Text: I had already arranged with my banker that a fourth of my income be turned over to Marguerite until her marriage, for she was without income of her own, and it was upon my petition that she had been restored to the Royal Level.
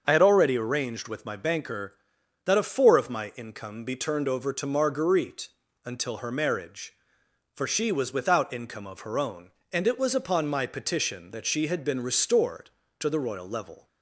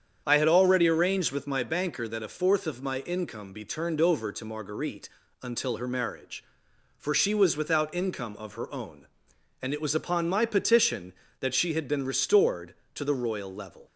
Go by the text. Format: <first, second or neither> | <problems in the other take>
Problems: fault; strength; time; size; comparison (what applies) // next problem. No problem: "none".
second | starts louder than the rest; until 1.0 s; 6.5 dB; strong in the second // says "four" for "fourth"; at 2.6 s // pauses between "Marguerite" and "until"; slight; at 5.4 s; 0.34 s long; slight in the second